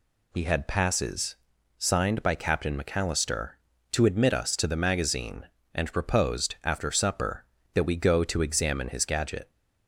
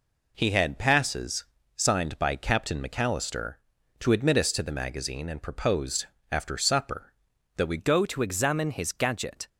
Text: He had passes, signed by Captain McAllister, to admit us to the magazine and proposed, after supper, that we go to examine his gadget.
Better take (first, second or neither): first